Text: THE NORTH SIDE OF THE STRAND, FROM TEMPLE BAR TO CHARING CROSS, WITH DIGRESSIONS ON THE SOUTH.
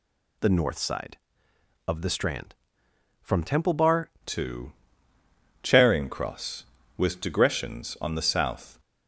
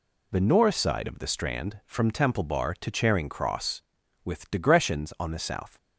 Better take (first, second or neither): second